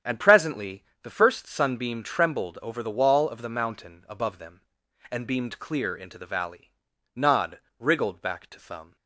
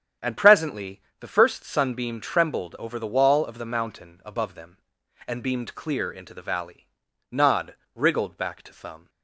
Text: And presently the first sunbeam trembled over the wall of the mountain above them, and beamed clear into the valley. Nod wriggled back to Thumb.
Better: neither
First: starts louder than the rest; strong; until 1.2 s; 8.5 dB // pauses between "presently" and "the"; slight; at 0.8 s; 0.20 s long // pauses between "Nod" and "wriggled"; slight; at 7.5 s; 0.20 s long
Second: starts louder than the rest; strong; until 1.4 s; 8.5 dB // pauses between "presently" and "the"; slight; at 1.0 s; 0.20 s long // pauses between "Nod" and "wriggled"; slight; at 7.7 s; 0.20 s long

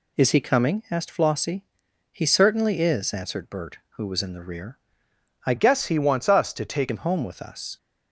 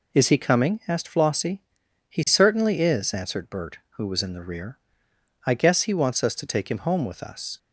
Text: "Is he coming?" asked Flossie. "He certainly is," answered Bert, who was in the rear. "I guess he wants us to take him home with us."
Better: second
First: changes voice from "guess" to "take"; from 5.5 to 6.8 s; 1.3 s long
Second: none

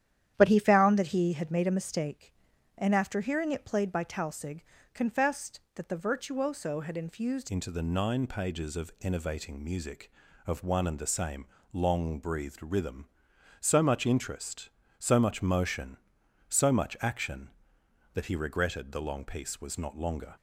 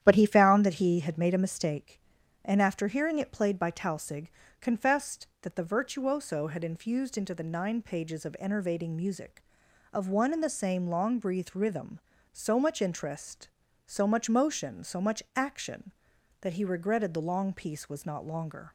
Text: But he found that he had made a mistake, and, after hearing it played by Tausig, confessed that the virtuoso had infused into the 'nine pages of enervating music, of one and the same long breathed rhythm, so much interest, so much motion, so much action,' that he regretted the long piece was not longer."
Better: second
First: starts louder than the rest; strong; until 1.3 s; 10.5 dB // changes voice at "into"; from 7.4 s on; 12.9 s long // pauses between "same" and "long"; slight; at 11.4 s; 0.26 s long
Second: starts louder than the rest; strong; until 1.0 s; 10.5 dB

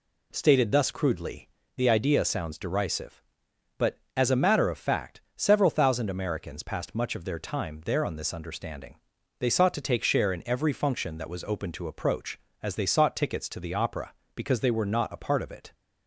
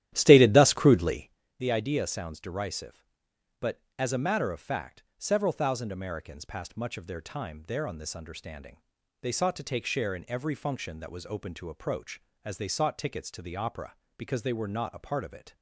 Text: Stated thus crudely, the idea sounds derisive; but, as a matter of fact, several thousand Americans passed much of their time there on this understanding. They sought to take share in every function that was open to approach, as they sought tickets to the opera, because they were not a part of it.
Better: first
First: none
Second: starts louder than the rest; strong; until 1.3 s; 12.5 dB

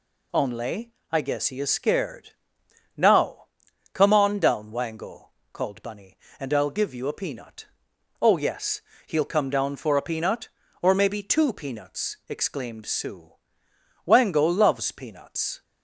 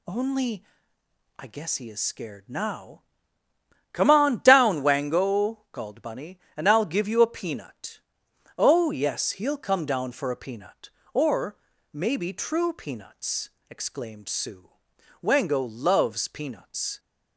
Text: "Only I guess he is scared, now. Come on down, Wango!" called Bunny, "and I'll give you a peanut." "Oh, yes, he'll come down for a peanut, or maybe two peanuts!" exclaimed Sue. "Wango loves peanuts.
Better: first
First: pauses between "Only" and "I"; slight; at 0.9 s; 0.18 s long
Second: pauses between "Only" and "I"; noticeable; at 0.6 s; 0.76 s long // pauses between "or" and "maybe"; slight; at 11.5 s; 0.34 s long // says "true" for "two"; at 12.3 s

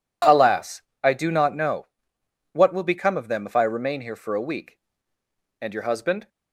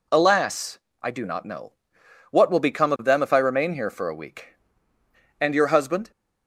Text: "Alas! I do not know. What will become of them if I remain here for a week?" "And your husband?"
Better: neither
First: none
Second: none

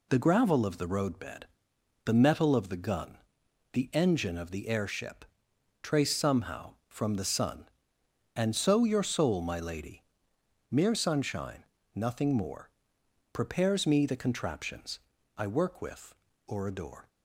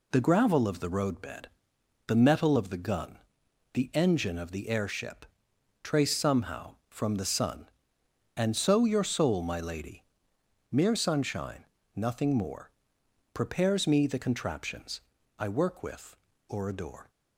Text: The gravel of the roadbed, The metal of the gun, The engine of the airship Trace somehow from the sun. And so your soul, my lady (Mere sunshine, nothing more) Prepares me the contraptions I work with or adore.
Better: neither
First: pauses between "airship" and "Trace"; noticeable; at 5.2 s; 0.58 s long // pauses between "contraptions" and "I"; slight; at 15.0 s; 0.36 s long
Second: pauses between "airship" and "Trace"; noticeable; at 5.2 s; 0.58 s long // pauses between "contraptions" and "I"; slight; at 15.0 s; 0.36 s long

